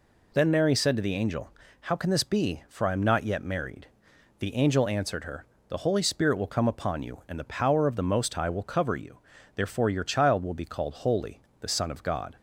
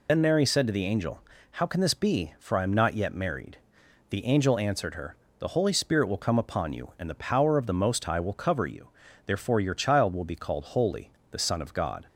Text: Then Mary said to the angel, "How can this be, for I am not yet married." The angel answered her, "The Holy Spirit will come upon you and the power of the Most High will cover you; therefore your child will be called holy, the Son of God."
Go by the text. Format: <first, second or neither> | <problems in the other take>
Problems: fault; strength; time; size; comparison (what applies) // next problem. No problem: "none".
first | loses the start of "Then"; at 0.0 s; 55 ms